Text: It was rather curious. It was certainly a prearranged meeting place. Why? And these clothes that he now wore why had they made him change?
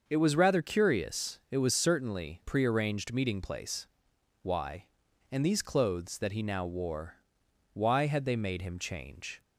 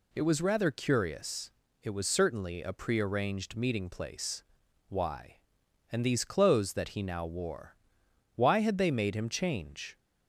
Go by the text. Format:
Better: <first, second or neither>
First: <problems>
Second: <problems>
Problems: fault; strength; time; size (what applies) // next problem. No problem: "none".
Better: second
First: starts louder than the rest; until 1.0 s; 6.5 dB // skips "a"; at 2.4 s // pauses between "wore" and "why"; noticeable; at 7.1 s; 0.58 s long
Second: pauses between "wore" and "why"; noticeable; at 7.7 s; 0.60 s long